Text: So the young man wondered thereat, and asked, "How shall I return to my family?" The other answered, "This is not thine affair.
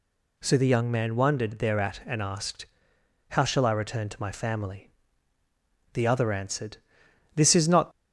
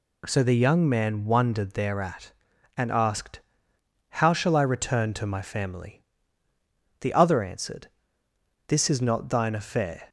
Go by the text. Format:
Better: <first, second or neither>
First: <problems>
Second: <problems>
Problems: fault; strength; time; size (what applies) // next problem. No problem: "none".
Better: second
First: stops before "thine affair"; at 7.9 s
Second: none